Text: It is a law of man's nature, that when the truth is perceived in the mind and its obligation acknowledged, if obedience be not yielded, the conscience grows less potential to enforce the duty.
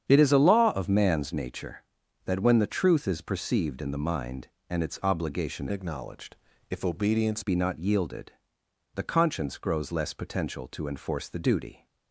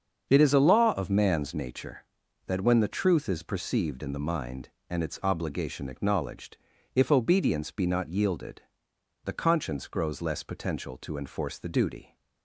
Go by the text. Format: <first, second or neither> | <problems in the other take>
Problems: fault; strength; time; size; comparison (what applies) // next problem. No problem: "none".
second | starts louder than the rest; strong; until 1.0 s; 8.5 dB; also in the second // changes voice from "acknowledged" to "obedience"; from 5.7 to 7.4 s; 1.7 s long